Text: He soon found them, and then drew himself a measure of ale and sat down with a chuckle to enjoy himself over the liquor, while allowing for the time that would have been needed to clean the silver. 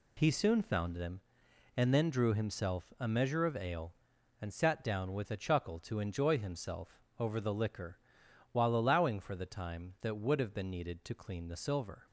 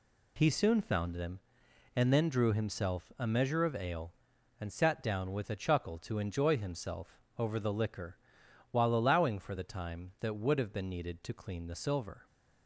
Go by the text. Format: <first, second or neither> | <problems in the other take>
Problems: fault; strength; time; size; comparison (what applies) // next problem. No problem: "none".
neither | pauses between "himself" and "over"; slight; the same in both